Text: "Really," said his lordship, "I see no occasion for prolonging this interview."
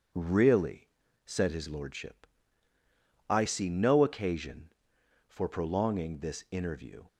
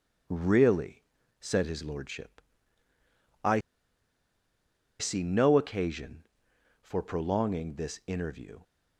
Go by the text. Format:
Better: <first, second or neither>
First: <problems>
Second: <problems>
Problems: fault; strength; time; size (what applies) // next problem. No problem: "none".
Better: first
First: none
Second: pauses between "I" and "see"; strong; at 3.6 s; 1.3 s long